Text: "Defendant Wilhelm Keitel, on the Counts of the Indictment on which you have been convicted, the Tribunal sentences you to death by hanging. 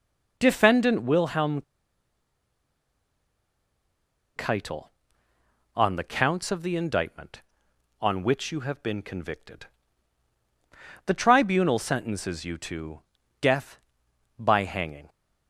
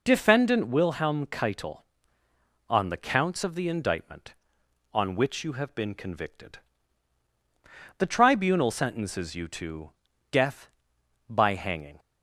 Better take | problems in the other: second | pauses between "Wilhelm" and "Keitel"; strong; at 1.6 s; 2.7 s long // pauses between "to" and "death"; slight; at 13.0 s; 0.36 s long; slight in the second

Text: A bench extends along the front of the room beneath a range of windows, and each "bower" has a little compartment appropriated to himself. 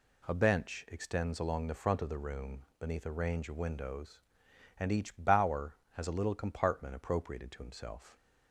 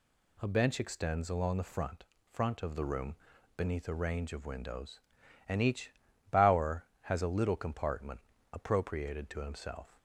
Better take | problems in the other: first | says "front" twice; at 2.3 s // pauses between "room" and "beneath"; at 3.1 s; 0.40 s long; slight in the first // pauses between "each" and "bower"; at 5.9 s; 0.40 s long // pauses between "compartment" and "appropriated"; slight; at 8.2 s; 0.32 s long

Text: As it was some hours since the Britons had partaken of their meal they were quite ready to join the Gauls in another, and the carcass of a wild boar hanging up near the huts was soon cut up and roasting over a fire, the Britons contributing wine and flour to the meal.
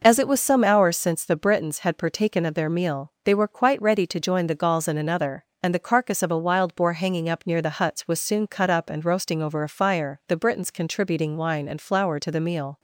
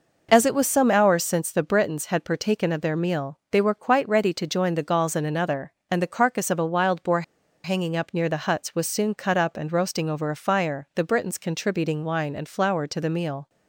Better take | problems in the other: first | pauses between "boar" and "hanging"; at 7.2 s; 0.42 s long

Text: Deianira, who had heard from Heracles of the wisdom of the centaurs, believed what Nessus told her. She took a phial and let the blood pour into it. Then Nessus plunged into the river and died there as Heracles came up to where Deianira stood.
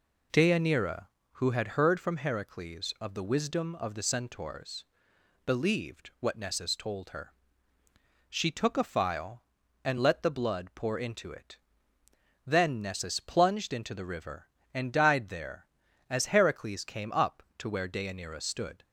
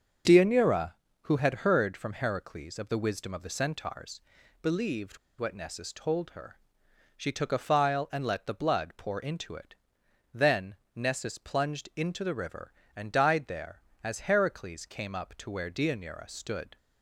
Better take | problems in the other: first | starts louder than the rest; until 1.5 s; 6.5 dB // pauses between "believed" and "what"; slight; at 5.1 s; 0.23 s long // pauses between "Then" and "Nessus"; slight; at 10.7 s; 0.18 s long

